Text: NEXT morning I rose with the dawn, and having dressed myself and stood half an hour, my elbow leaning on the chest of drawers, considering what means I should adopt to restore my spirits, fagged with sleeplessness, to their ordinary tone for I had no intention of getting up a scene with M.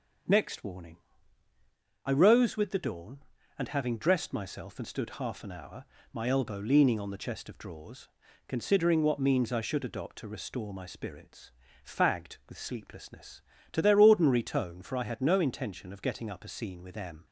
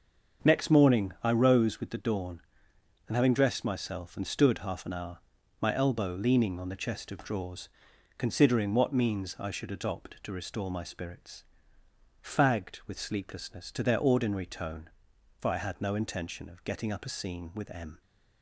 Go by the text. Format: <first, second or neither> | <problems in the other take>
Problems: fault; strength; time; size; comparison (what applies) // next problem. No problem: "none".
second | starts louder than the rest; until 2.3 s; 7 dB; also in the second // says "warning" for "morning"; at 0.6 s